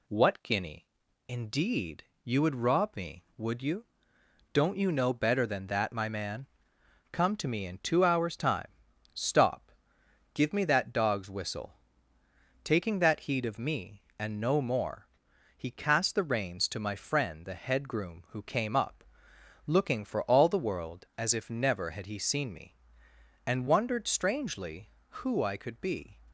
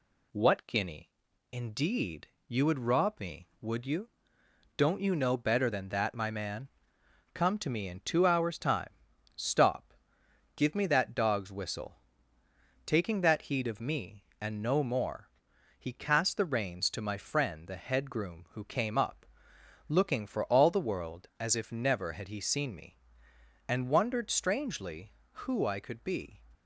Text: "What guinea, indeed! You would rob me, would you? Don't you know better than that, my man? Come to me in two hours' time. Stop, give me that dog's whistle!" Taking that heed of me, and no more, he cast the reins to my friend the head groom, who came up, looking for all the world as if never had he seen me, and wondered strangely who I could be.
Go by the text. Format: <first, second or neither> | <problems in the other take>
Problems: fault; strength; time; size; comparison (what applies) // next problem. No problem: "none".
neither | none